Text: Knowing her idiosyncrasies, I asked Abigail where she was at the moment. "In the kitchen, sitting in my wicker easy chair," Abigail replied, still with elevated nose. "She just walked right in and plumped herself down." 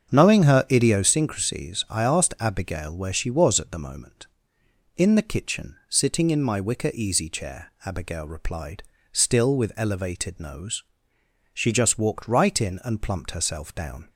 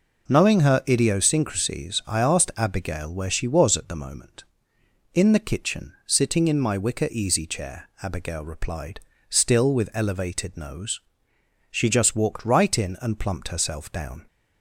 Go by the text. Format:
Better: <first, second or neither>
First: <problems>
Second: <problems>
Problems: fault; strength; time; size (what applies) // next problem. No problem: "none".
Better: second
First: starts louder than the rest; strong; until 1.2 s; 7.5 dB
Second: none